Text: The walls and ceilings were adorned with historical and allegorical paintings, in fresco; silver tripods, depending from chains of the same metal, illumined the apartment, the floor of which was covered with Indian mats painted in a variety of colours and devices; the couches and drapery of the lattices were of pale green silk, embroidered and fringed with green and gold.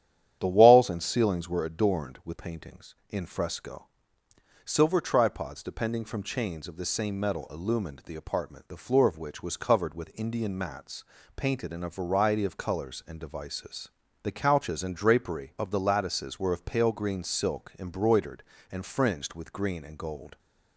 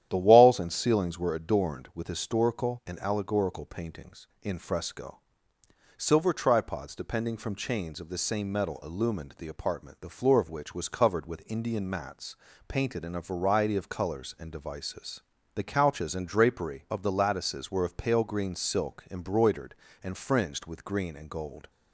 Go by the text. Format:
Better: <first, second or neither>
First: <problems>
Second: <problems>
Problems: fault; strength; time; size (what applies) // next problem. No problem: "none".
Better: second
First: starts louder than the rest; strong; until 1.4 s; 10 dB // skips "historical and allegorical"; at 2.3 s // pauses between "mats" and "painted"; slight; at 11.0 s; 0.32 s long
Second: starts louder than the rest; strong; until 1.1 s; 11 dB // pauses between "mats" and "painted"; slight; at 12.3 s; 0.32 s long